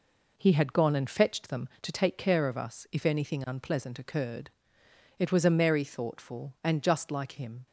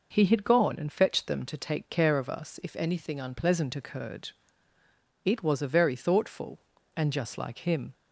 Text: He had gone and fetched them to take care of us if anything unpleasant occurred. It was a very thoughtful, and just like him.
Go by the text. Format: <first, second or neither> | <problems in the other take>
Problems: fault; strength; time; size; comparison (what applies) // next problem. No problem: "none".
second | says "merry" for "very"; at 5.4 s